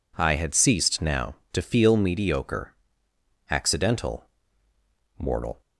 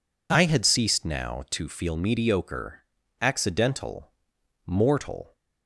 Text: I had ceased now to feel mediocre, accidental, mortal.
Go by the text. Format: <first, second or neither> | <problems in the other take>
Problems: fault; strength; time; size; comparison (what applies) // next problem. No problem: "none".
neither | none